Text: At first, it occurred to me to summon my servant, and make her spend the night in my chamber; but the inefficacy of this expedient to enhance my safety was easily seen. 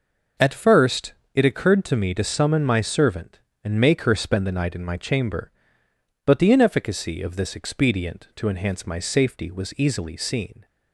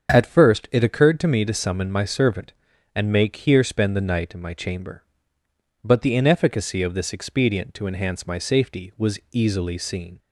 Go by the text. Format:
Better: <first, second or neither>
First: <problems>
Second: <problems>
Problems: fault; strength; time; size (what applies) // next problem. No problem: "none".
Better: first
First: none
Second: starts louder than the rest; strong; until 1.1 s; 7.5 dB // says "here" for "her"; at 3.3 s